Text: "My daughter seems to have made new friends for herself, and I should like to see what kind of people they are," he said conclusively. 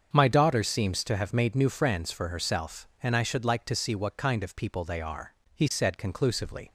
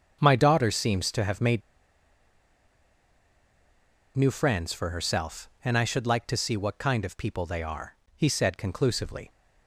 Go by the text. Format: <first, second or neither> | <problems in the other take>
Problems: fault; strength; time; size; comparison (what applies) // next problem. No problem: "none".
first | starts louder than the rest; until 1.2 s; 7 dB; also in the first // pauses between "made" and "new"; strong; at 1.6 s; 2.5 s long